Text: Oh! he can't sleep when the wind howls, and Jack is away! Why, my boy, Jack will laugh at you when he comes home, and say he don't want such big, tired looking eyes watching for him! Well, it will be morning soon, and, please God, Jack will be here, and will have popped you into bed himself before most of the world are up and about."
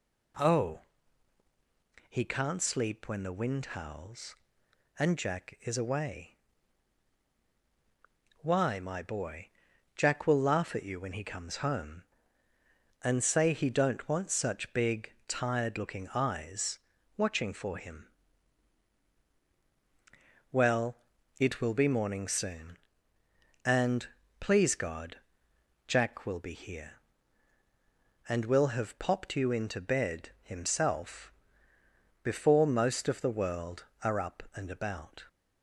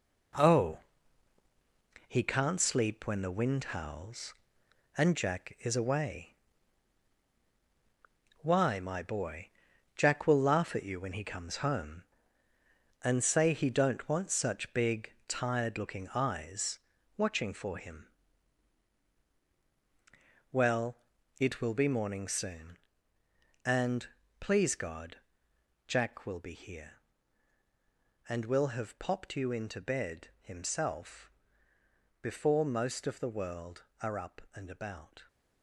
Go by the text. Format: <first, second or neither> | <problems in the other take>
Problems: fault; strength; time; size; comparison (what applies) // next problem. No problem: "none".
first | gets quieter; strong; throughout; 7.5 dB // pauses between "eyes" and "watching"; at 16.7 s; 0.38 s long; also in the first // pauses between "himself" and "before"; noticeable; at 31.3 s; 0.90 s long; noticeable in the first